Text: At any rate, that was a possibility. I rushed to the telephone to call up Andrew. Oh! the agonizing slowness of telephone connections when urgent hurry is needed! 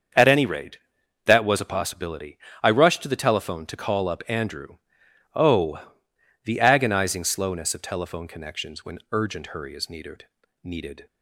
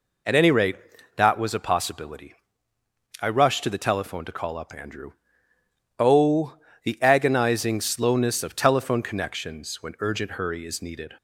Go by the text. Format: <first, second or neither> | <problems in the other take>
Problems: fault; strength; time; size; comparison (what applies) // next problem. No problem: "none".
second | starts louder than the rest; until 1.5 s; 7 dB // says "needed" twice; at 10.6 s